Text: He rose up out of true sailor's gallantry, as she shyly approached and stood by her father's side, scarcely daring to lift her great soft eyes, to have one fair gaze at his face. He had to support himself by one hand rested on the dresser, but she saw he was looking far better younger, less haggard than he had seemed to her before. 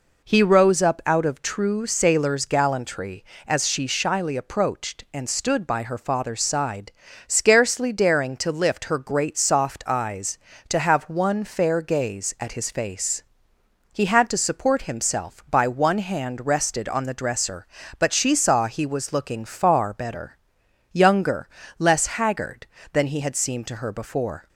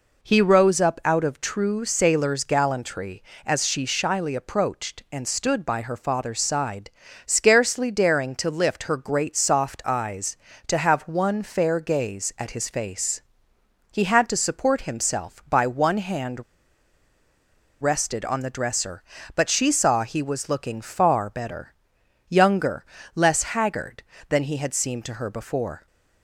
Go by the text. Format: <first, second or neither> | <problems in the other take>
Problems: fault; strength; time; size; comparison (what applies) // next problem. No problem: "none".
first | pauses between "hand" and "rested"; strong; at 16.4 s; 1.3 s long // pauses between "better" and "younger"; noticeable; at 21.7 s; 0.56 s long; noticeable in the first